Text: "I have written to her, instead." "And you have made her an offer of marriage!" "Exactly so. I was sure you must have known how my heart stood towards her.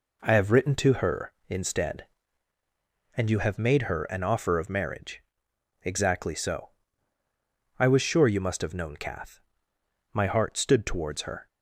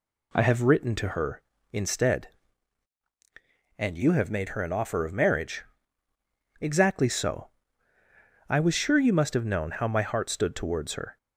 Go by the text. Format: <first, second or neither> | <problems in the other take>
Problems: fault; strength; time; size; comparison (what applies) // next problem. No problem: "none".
second | says "kath" for "how"; at 8.9 s